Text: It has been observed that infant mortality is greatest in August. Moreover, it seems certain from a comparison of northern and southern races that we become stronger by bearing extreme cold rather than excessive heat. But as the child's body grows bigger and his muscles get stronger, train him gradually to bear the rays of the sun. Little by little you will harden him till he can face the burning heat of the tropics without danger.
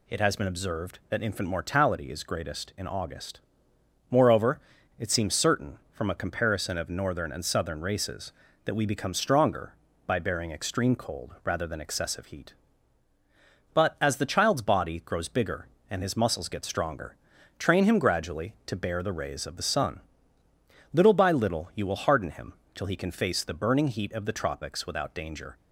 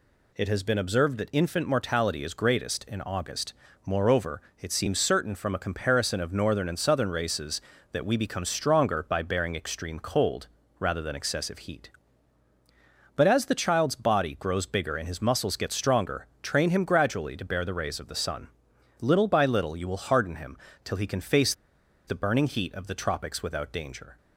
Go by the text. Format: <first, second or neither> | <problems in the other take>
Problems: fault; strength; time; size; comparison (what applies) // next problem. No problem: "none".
first | pauses between "cold" and "rather"; slight; at 10.4 s; 0.32 s long // pauses between "him" and "till"; slight; at 20.5 s; 0.26 s long; slight in the first // pauses between "face" and "the"; noticeable; at 21.5 s; 0.54 s long